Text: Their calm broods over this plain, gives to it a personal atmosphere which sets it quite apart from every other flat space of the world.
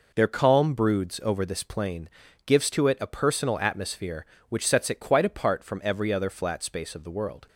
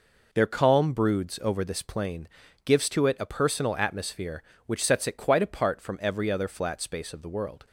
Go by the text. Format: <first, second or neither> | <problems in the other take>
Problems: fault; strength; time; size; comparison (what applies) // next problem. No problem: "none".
neither | none